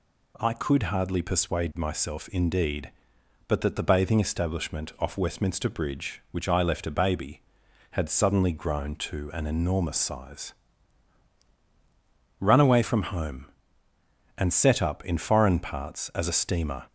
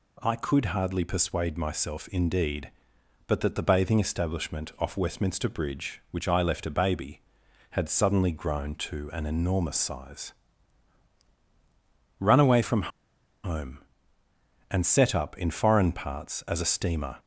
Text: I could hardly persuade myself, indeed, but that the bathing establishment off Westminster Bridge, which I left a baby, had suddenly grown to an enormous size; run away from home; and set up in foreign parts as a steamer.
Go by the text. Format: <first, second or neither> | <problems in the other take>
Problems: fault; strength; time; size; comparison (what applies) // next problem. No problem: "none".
first | pauses between "from" and "home"; noticeable; at 12.9 s; 0.53 s long